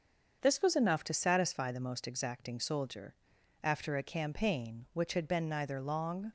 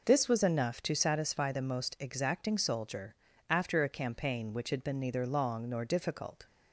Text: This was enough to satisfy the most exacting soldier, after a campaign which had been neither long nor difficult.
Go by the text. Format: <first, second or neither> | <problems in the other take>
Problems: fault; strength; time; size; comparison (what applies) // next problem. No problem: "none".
second | starts louder than the rest; until 1.4 s; 6.5 dB // stops before "nor difficult"; at 6.2 s